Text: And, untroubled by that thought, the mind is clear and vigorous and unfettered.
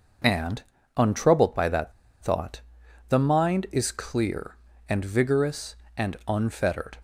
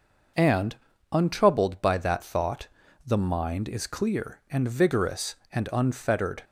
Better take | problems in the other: second | pauses between "that" and "thought"; slight; at 1.9 s; 0.30 s long

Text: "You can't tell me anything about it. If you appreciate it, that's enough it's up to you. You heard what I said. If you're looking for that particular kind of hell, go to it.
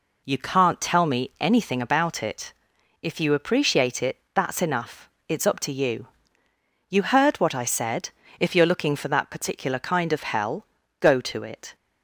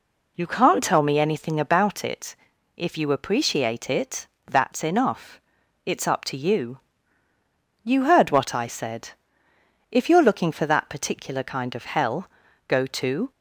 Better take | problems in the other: first | pauses between "enough" and "it's"; at 5.4 s; 0.44 s long; slight in the first // stops before "it"; at 13.3 s

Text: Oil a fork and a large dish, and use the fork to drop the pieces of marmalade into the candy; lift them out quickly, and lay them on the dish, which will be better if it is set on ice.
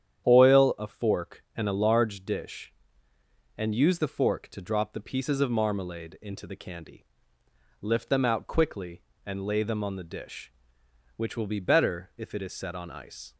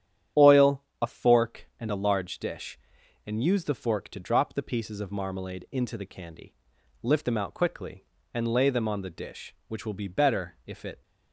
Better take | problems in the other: first | starts louder than the rest; strong; until 1.5 s; 10 dB; strong in the first // pauses between "Oil" and "a"; slight; at 0.8 s; 0.20 s long // stops before "is set on ice"; at 11.0 s

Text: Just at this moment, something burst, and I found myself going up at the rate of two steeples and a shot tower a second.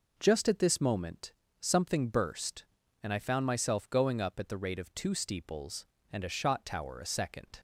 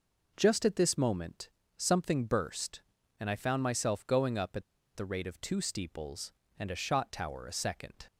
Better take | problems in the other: first | pauses between "at" and "the"; slight; at 4.6 s; 0.33 s long

